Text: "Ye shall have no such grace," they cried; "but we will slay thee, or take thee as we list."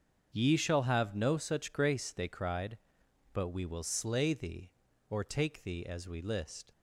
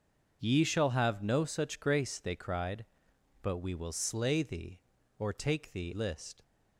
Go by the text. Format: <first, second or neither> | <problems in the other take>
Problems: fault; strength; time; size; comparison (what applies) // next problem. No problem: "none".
first | starts louder than the rest; until 1.4 s; 6.5 dB; also in the first // skips "as we"; at 5.9 s